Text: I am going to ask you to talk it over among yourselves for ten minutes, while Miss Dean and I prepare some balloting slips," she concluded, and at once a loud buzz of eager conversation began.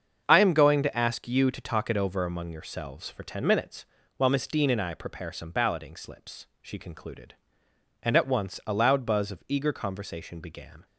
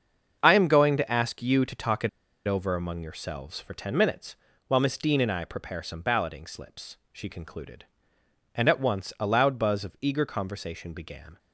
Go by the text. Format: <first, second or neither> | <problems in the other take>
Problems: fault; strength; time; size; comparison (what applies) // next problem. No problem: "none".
first | starts louder than the rest; until 1.4 s; 7 dB; also in the first // pauses between "it" and "over"; at 2.0 s; 0.38 s long